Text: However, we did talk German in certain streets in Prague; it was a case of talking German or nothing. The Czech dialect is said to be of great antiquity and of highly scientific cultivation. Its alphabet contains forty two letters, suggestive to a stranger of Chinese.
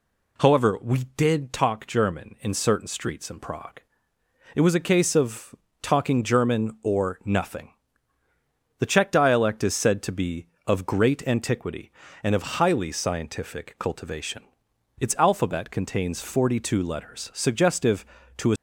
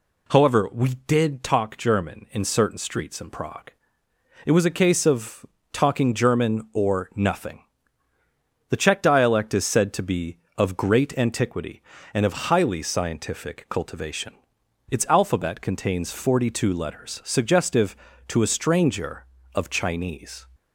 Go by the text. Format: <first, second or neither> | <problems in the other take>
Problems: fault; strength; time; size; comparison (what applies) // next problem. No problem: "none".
second | pauses between "of" and "talking"; slight; at 5.5 s; 0.28 s long; slight in the second // stops before "stranger of Chinese"; at 18.5 s